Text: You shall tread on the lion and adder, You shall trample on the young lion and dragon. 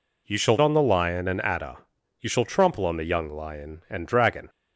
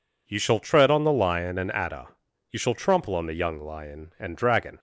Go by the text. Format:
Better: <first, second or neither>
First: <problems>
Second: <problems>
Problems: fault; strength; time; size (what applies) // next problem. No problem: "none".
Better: second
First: skips "tread"; at 0.5 s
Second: none